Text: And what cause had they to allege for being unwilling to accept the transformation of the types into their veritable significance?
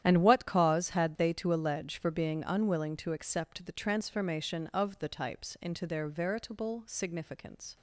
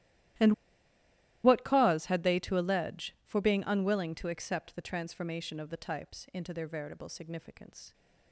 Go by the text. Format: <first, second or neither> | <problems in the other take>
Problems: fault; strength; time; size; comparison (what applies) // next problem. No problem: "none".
first | starts louder than the rest; strong; until 2.3 s; 14 dB; strong in the first // pauses between "And" and "what"; noticeable; at 0.5 s; 0.91 s long